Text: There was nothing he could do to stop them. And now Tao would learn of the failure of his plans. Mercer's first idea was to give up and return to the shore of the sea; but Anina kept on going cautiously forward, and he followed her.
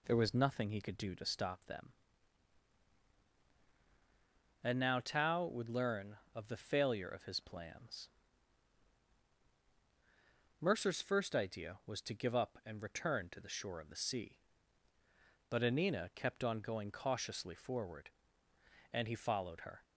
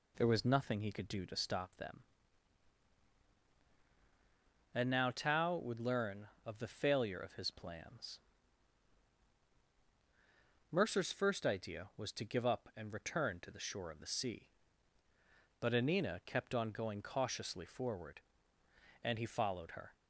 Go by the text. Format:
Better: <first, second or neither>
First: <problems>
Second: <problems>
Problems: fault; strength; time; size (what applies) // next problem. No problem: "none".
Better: neither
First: none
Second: none